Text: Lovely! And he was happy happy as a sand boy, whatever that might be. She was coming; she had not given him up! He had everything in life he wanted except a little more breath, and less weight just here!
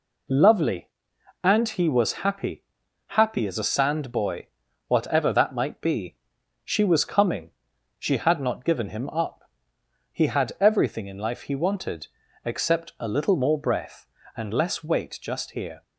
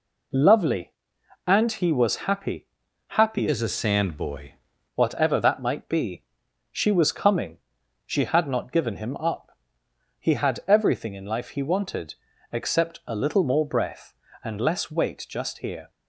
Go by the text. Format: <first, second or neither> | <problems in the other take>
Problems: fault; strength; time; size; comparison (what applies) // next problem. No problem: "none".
first | pauses between "happy" and "happy"; noticeable; at 2.6 s; 0.46 s long; noticeable in the first // changes voice from "as" to "boy"; from 3.4 to 4.5 s; 1.1 s long // pauses between "wanted" and "except"; slight; at 12.1 s; 0.36 s long; slight in the first